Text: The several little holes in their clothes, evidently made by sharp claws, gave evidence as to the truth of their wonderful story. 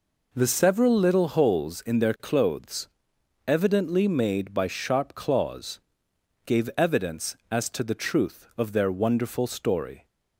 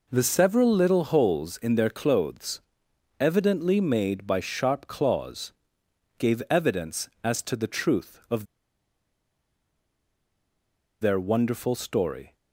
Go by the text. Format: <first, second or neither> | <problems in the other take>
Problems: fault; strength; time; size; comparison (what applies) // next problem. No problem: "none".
first | pauses between "of" and "their"; strong; at 8.4 s; 2.5 s long